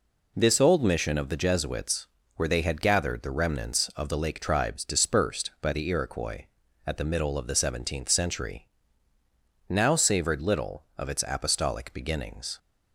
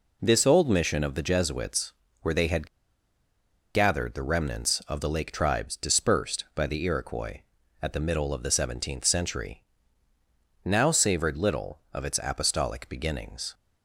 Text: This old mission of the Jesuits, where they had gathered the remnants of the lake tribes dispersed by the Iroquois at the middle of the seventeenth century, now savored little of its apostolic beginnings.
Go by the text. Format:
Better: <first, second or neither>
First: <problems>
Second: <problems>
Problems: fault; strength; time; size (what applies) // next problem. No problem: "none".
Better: first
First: none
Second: pauses between "had" and "gathered"; at 2.6 s; 1.0 s long